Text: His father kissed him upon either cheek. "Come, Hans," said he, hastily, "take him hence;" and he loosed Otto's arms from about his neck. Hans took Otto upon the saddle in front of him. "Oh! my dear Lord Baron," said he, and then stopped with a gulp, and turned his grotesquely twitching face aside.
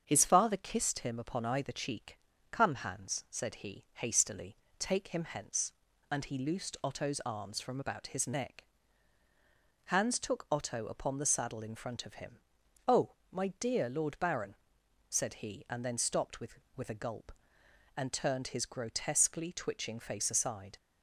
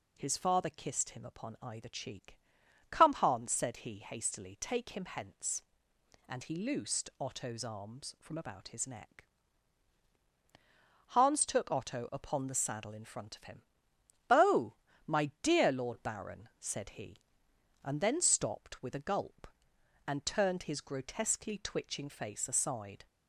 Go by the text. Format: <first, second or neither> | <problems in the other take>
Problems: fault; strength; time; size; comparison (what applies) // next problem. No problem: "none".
second | starts louder than the rest; strong; until 1.0 s; 7 dB // says "with" twice; at 16.7 s